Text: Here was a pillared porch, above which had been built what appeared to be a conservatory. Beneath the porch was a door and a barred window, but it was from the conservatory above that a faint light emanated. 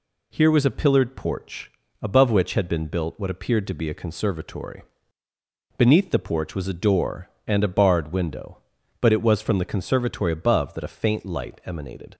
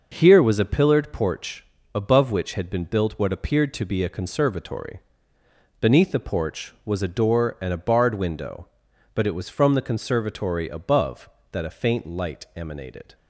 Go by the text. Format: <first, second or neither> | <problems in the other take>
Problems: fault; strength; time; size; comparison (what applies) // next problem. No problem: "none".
neither | none